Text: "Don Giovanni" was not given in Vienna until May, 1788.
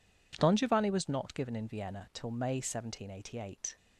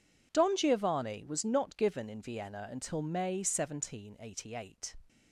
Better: second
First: says "till" for "until"; at 2.1 s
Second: none

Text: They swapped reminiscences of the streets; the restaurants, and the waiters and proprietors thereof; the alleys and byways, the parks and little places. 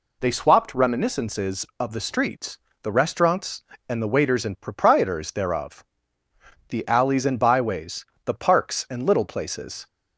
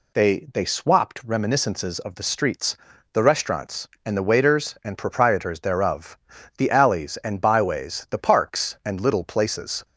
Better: first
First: none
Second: says "They" twice; at 0.5 s

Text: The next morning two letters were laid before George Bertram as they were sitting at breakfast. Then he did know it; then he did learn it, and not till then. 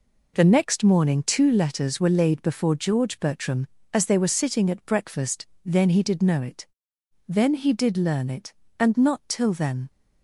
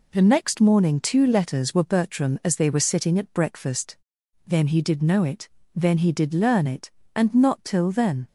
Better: first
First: none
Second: skips "laid before George"; at 1.8 s

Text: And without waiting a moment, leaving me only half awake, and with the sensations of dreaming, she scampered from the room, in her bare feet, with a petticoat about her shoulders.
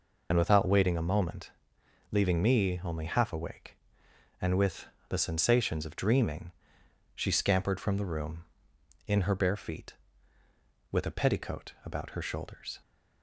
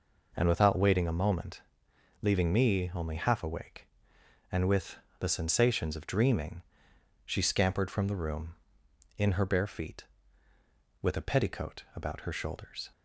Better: second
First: loses the start of "And"; at 0.3 s; 75 ms // pauses between "with" and "the"; slight; at 4.8 s; 0.22 s long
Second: pauses between "with" and "the"; slight; at 4.9 s; 0.22 s long

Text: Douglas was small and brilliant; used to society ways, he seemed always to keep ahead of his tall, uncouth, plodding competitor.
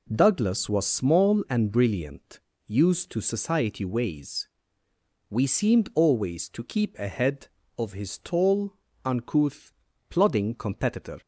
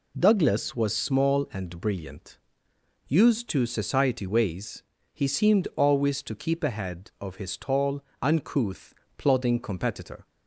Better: second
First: says "we" for "he"; at 5.3 s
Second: none

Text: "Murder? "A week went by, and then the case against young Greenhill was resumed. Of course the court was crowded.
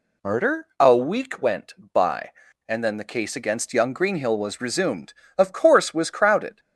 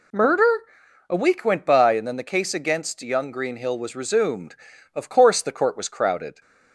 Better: second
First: skips "the court"; at 5.9 s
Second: none

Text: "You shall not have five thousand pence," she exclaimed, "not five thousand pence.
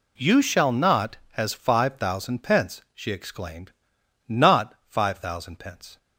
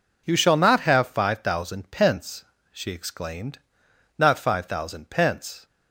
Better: second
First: says "has" for "have"; at 1.3 s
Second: none

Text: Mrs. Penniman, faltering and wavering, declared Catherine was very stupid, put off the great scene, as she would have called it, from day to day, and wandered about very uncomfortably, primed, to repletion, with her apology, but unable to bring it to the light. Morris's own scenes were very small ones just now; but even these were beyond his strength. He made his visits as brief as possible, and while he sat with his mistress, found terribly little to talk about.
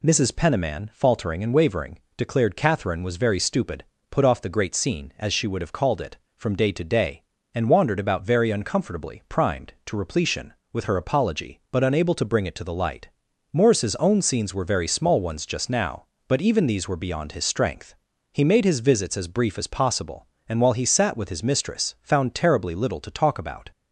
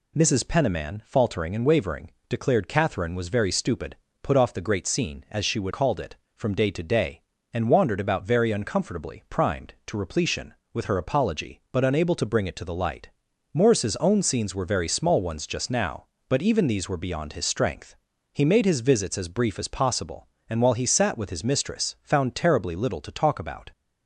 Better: first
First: none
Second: skips "have"; at 5.7 s

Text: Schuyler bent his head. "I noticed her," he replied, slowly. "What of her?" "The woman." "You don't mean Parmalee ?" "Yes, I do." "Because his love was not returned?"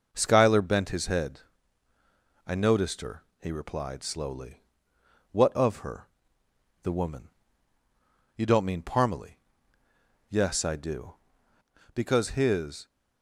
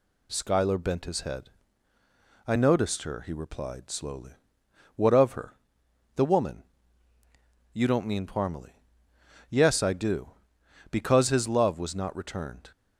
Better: second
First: starts louder than the rest; noticeable; until 1.1 s; 6 dB // stops before "love was not returned"; at 12.8 s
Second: none

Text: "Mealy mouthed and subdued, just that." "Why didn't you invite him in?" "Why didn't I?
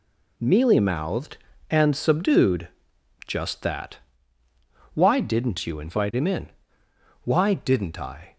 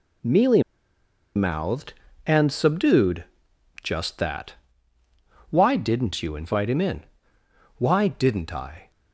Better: first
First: none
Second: pauses between "Mealy" and "mouthed"; noticeable; at 0.6 s; 0.74 s long

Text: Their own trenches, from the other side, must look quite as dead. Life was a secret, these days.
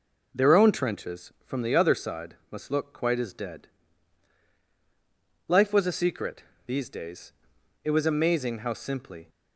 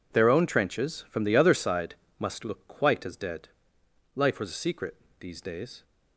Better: second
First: goes on to say "It was amazing how simply"; from 7.8 s on; 1.4 s long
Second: none

